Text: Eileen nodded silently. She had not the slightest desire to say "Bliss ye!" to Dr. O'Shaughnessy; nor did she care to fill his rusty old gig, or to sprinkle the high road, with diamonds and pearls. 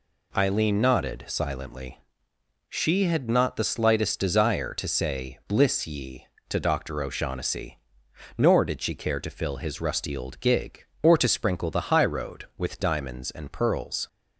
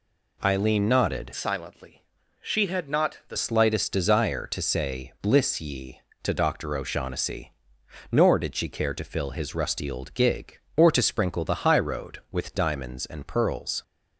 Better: first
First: none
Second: changes voice from "silently" to "the"; from 1.3 to 3.3 s; 2.0 s long

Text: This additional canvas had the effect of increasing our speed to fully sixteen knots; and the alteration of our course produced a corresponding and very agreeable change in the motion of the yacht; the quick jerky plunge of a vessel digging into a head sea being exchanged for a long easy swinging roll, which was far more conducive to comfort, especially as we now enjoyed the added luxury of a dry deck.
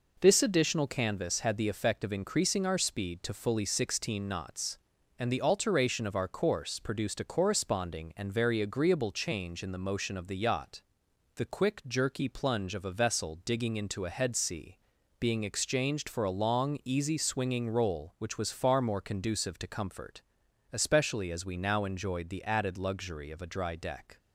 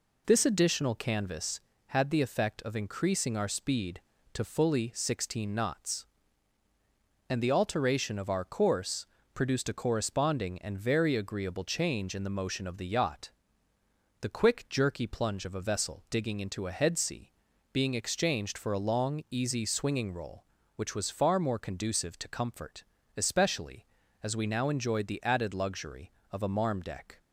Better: first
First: pauses between "sea" and "being"; at 14.7 s; 0.42 s long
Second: pauses between "course" and "produced"; slight; at 9.0 s; 0.30 s long // pauses between "sea" and "being"; at 17.3 s; 0.40 s long // says "marm" for "dry"; at 26.4 s

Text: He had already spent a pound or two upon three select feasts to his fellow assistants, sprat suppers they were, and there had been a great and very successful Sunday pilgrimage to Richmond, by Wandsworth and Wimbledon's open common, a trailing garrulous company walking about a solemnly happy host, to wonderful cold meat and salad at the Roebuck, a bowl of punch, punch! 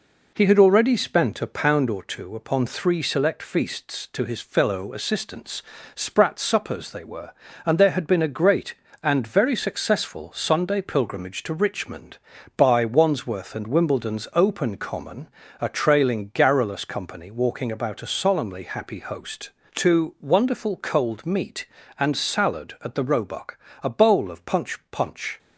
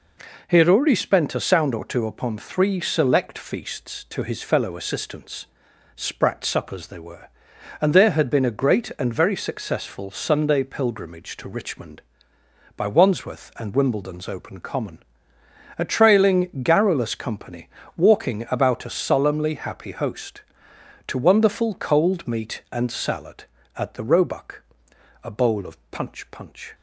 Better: first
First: none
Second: says "sound" for "pound"; at 1.4 s // pauses between "company" and "walking"; slight; at 17.6 s; 0.28 s long // pauses between "of" and "punch"; slight; at 25.7 s; 0.16 s long

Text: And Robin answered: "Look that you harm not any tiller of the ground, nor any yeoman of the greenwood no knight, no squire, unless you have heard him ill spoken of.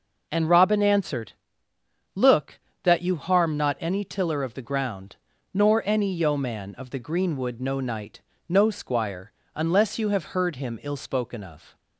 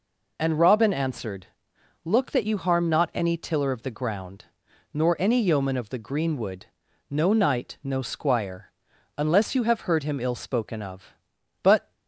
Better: first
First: none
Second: pauses between "greenwood" and "no"; noticeable; at 6.6 s; 0.46 s long // goes on to say "But"; slight; from 11.6 s on; 0.32 s long

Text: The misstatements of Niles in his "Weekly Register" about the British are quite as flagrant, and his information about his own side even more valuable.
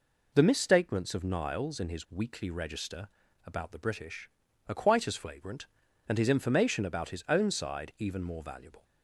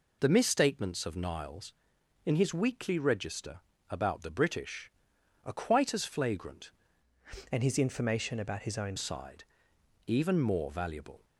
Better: first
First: pauses between "Register" and "about"; slight; at 3.0 s; 0.36 s long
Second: pauses between "Register" and "about"; slight; at 3.5 s; 0.30 s long // changes voice from "and" to "own"; from 7.5 to 8.9 s; 1.4 s long // pauses between "side" and "even"; noticeable; at 9.4 s; 0.62 s long

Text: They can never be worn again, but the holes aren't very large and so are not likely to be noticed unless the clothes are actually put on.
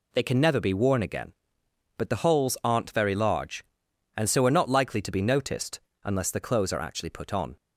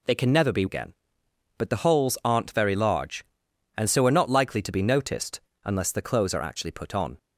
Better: first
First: pauses between "noticed" and "unless"; slight; at 5.7 s; 0.24 s long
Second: skips "worn"; at 0.6 s // pauses between "noticed" and "unless"; slight; at 5.3 s; 0.24 s long

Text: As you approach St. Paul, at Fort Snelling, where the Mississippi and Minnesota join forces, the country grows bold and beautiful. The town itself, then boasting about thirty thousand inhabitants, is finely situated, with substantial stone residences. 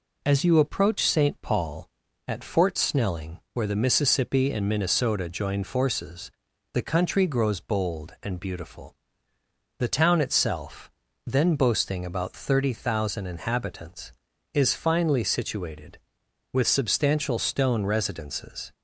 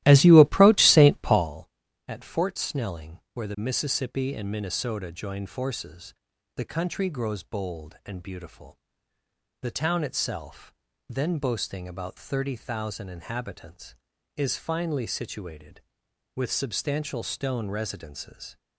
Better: first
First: none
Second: starts louder than the rest; strong; until 1.6 s; 15 dB

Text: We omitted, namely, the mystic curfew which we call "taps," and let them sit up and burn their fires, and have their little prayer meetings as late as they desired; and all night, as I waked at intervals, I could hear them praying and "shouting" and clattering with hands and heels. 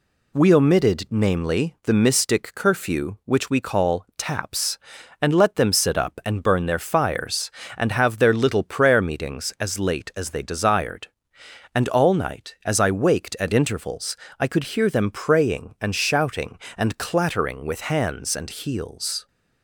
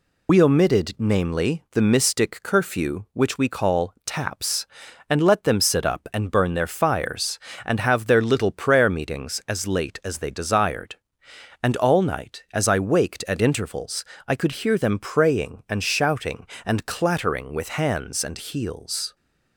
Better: first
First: none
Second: loses the start of "We"; at 0.2 s; 65 ms

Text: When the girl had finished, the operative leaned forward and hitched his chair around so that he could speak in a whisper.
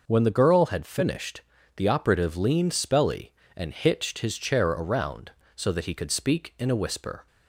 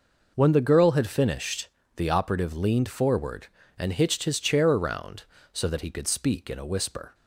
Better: second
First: says "spelly" for "forward"; at 2.7 s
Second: none

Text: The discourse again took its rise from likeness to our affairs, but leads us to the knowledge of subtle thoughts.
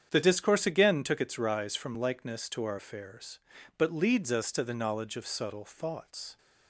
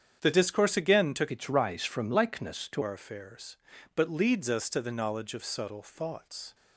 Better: first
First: starts louder than the rest; strong; until 1.1 s; 8 dB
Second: starts louder than the rest; strong; until 1.2 s; 8.5 dB // changes voice from "its" to "to"; from 1.3 to 2.8 s; 1.5 s long

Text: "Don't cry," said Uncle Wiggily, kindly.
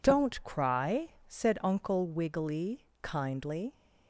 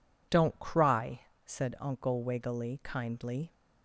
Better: neither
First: none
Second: none

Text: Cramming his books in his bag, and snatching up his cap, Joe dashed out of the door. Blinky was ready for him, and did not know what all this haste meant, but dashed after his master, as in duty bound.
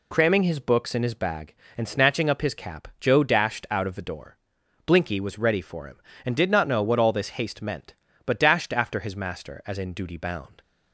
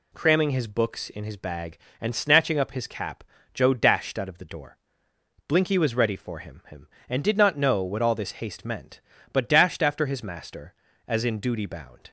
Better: first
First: none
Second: says "him" twice; at 6.6 s

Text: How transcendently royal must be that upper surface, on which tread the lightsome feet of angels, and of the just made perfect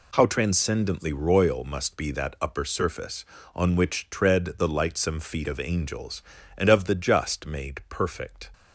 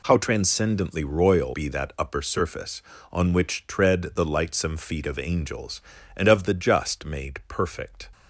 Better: first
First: none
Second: skips "must"; at 1.5 s

